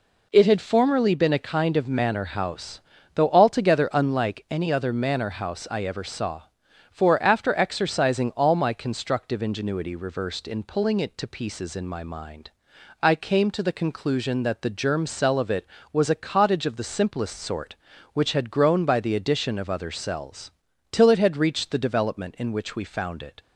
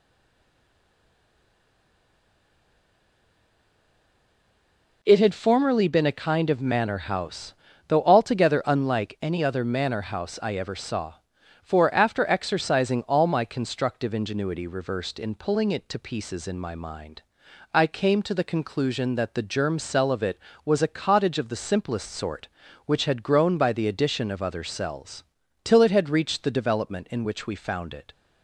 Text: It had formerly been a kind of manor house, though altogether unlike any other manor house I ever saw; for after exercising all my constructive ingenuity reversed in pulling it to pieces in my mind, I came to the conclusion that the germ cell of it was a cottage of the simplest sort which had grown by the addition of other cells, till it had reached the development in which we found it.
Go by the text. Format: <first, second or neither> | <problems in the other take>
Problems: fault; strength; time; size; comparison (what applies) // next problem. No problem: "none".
first | stays silent before the first word; strong; until 5.0 s; 5.0 s long